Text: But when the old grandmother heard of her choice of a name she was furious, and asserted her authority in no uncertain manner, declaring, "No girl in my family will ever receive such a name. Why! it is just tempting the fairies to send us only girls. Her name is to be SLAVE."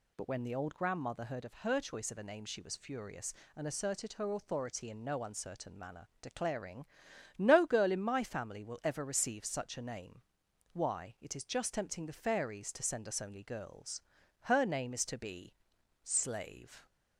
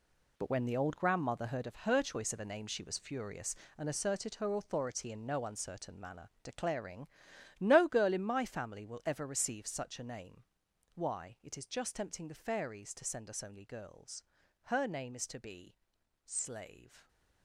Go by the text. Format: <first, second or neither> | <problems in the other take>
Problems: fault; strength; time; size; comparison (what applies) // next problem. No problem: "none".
first | gets quieter; strong; throughout; 10.5 dB // pauses between "be" and "SLAVE"; noticeable; at 15.7 s; 0.52 s long; noticeable in the first